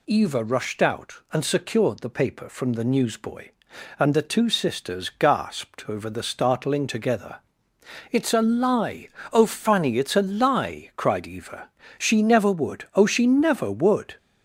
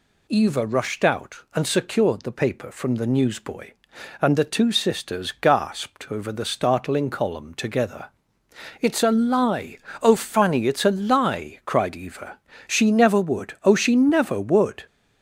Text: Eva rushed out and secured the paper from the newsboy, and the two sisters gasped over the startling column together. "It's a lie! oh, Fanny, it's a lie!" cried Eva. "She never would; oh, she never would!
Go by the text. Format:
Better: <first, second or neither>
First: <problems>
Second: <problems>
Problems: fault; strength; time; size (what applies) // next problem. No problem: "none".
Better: second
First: skips "column"; at 6.8 s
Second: none